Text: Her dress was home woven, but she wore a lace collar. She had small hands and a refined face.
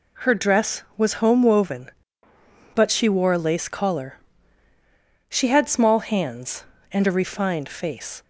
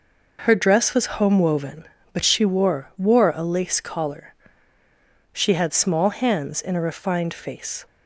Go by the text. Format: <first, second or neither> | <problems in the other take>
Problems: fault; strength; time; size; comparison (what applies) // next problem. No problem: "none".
first | says "wore" twice; at 2.9 s